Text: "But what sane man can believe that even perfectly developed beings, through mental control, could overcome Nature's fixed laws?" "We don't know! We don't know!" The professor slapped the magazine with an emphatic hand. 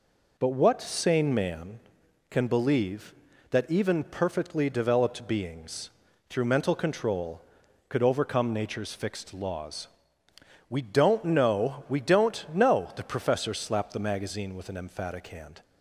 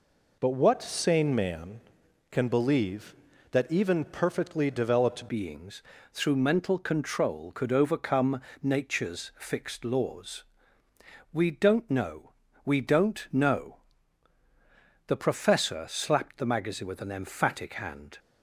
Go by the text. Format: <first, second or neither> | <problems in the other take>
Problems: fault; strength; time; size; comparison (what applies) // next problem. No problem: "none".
first | changes voice at "beings"; from 5.2 s on; 12.9 s long // pauses between "overcome" and "Nature's"; slight; at 8.4 s; 0.20 s long